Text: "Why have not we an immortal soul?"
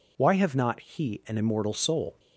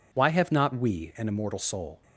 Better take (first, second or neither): second